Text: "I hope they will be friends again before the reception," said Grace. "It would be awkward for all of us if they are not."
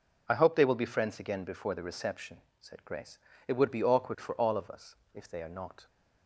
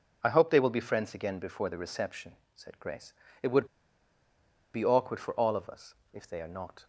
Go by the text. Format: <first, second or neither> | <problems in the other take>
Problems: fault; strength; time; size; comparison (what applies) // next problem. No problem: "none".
first | pauses between "would" and "be"; at 3.6 s; 1.0 s long // pauses between "us" and "if"; slight; at 5.9 s; 0.18 s long; slight in the first